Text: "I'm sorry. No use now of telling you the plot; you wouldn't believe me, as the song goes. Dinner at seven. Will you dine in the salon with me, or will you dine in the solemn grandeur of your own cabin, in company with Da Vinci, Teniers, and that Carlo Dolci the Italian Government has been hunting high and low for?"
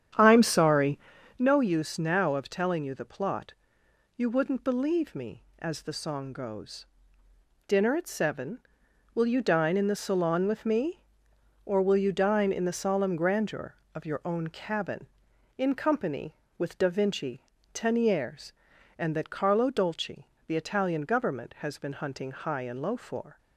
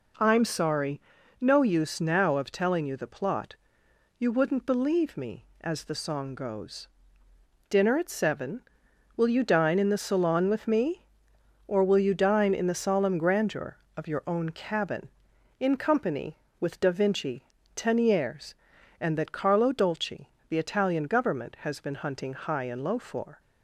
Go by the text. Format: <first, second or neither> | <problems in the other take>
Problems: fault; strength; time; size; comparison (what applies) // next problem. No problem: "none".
second | starts louder than the rest; strong; until 1.5 s; 9 dB // pauses between "Dolci" and "the"; slight; at 20.2 s; 0.20 s long; slight in the second